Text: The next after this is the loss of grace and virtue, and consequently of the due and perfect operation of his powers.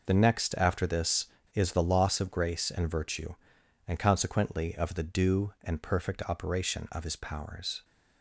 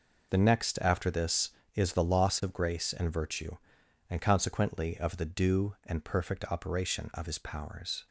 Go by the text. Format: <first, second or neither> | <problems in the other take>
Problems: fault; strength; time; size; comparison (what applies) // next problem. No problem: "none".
neither | none